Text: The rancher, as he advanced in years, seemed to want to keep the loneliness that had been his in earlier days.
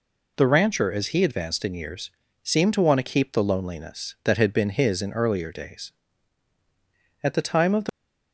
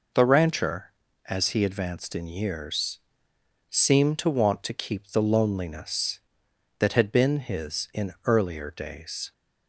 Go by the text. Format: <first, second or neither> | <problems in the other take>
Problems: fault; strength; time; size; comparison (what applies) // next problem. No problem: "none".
second | goes on to say "At the time of the"; noticeable; from 7.2 s on; 0.70 s long